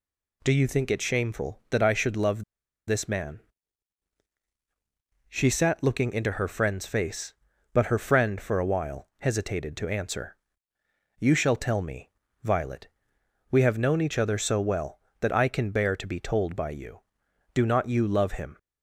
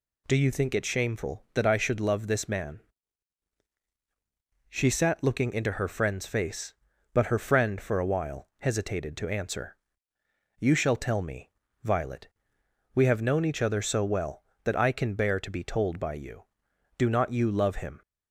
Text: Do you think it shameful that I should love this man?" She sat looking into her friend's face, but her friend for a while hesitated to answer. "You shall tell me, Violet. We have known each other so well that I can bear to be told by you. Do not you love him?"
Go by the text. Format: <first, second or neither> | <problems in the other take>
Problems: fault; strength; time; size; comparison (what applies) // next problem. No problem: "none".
second | pauses between "love" and "this"; at 2.4 s; 0.43 s long